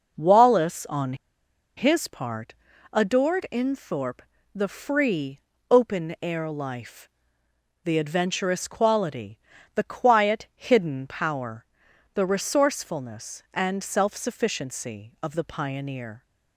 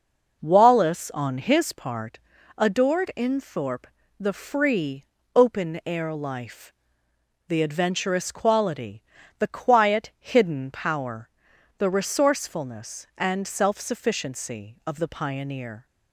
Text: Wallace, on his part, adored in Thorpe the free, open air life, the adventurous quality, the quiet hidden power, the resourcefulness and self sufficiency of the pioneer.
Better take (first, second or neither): second